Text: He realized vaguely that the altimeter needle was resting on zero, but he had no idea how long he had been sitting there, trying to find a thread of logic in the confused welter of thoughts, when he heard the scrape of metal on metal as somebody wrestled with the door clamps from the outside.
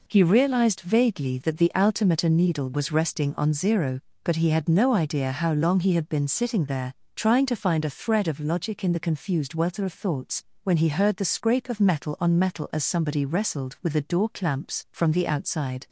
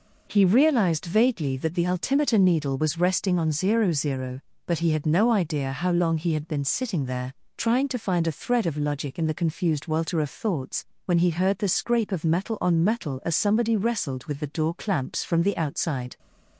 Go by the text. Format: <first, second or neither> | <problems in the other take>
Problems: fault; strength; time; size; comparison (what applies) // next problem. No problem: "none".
first | says "zero" twice; at 3.9 s